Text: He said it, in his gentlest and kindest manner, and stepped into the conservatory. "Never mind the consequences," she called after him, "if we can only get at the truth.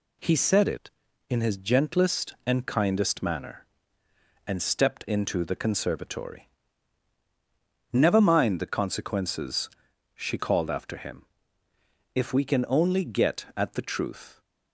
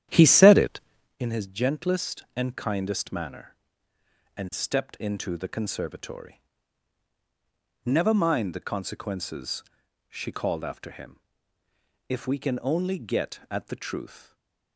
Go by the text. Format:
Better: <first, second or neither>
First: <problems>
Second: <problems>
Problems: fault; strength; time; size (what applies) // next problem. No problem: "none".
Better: first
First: none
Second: starts louder than the rest; strong; until 1.2 s; 10.5 dB // stays silent after the last word; slight; from 14.1 s on; 0.6 s long